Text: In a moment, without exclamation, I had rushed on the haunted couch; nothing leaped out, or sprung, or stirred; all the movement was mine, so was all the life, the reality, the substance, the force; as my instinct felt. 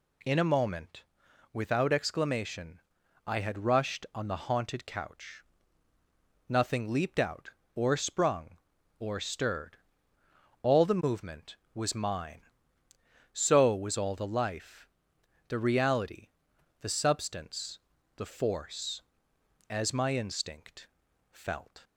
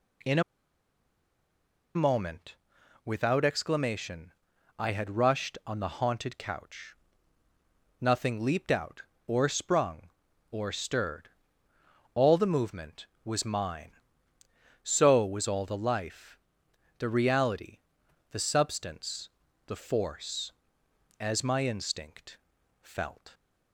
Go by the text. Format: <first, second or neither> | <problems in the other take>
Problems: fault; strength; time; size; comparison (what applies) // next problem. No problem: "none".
first | pauses between "a" and "moment"; strong; at 0.4 s; 1.5 s long // pauses between "instinct" and "felt"; at 22.3 s; 0.44 s long; also in the first